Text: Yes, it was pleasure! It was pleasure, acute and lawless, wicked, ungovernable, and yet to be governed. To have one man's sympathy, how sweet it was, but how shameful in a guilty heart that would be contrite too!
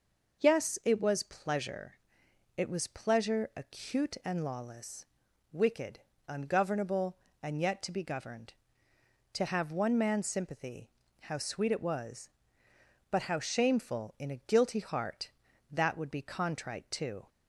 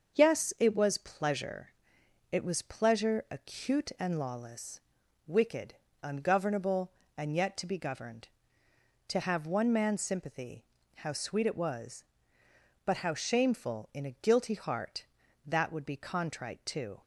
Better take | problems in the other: first | gets quieter; noticeable; throughout; 5 dB

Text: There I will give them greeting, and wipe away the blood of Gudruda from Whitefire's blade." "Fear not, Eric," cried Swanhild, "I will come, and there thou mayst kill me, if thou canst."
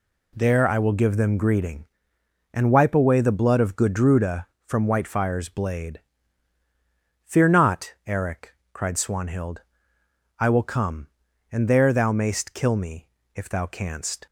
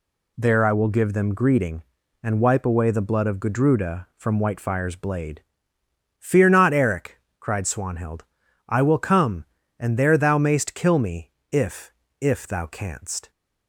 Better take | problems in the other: first | says "if" twice; at 12.1 s

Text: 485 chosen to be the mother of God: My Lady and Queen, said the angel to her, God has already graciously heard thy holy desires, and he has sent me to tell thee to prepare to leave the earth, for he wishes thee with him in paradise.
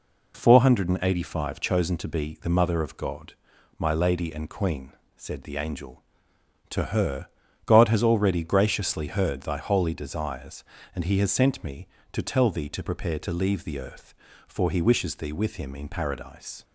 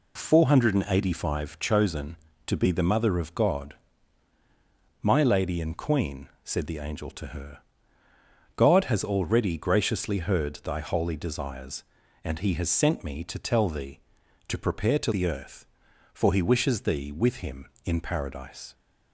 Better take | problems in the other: first | skips "leave"; at 15.1 s

